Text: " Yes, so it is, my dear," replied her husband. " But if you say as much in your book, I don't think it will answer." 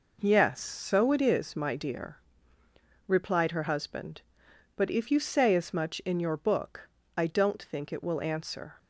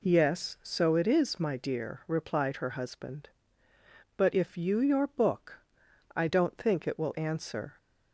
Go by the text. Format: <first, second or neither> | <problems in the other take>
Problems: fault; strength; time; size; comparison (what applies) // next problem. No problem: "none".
first | skips "say as much in"; at 4.8 s